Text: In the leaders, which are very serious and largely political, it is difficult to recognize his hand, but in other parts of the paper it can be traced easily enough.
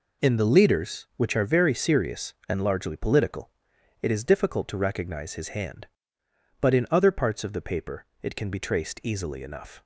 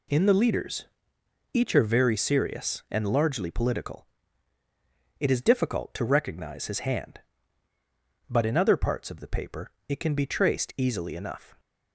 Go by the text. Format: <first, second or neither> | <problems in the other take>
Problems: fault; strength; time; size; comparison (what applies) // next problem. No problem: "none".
first | says "each" for "which"; at 1.5 s // pauses between "paper" and "it"; slight; at 9.6 s; 0.18 s long; slight in the first